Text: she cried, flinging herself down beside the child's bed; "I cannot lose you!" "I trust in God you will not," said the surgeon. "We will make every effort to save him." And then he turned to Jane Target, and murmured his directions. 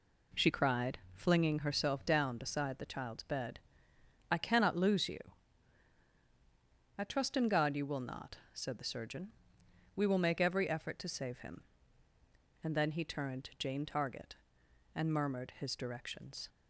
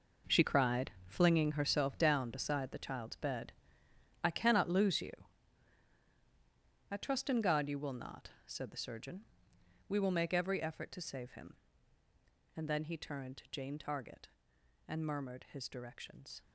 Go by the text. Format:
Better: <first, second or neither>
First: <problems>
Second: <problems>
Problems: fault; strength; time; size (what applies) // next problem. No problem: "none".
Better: first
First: none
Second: gets quieter; strong; throughout; 12.5 dB